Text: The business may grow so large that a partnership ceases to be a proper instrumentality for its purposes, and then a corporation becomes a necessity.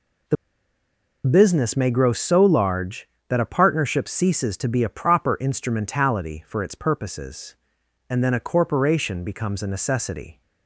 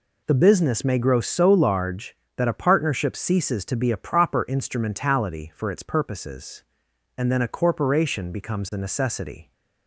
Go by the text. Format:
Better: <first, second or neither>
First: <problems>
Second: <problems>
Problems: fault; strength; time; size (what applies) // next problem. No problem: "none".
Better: second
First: pauses between "The" and "business"; noticeable; at 0.3 s; 0.90 s long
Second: none